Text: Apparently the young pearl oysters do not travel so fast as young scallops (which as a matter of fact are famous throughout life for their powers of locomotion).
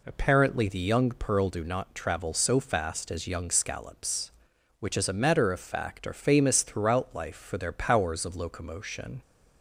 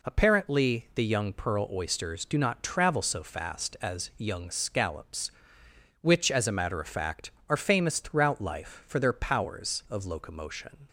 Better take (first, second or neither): second